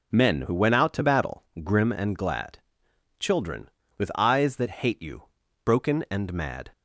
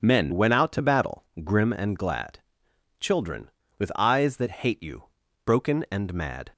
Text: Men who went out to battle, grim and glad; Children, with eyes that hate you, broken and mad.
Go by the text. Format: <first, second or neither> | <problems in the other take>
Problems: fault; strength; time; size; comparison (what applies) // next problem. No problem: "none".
first | skips "who"; at 0.3 s